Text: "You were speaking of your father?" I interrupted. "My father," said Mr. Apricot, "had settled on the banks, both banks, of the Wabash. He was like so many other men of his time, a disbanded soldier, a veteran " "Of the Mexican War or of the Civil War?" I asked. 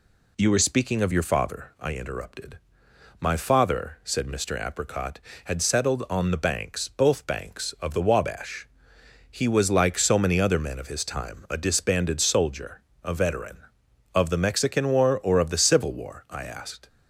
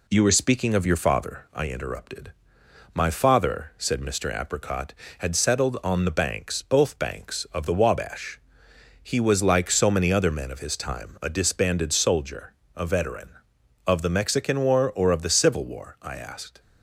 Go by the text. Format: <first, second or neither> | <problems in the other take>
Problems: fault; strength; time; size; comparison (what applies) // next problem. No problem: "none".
first | gets quieter; slight; throughout; 3 dB